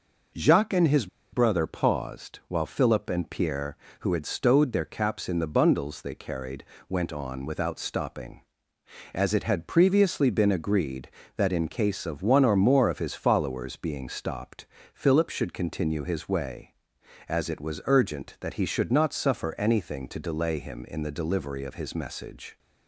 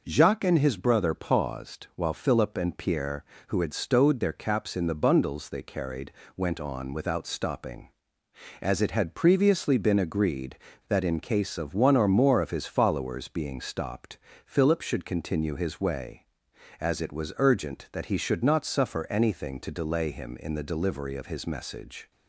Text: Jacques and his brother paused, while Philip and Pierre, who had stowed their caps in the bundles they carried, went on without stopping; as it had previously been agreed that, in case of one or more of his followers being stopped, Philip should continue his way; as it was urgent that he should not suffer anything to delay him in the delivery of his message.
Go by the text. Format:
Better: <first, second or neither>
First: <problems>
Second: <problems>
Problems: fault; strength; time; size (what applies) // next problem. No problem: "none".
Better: second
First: pauses between "his" and "brother"; slight; at 1.0 s; 0.25 s long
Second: none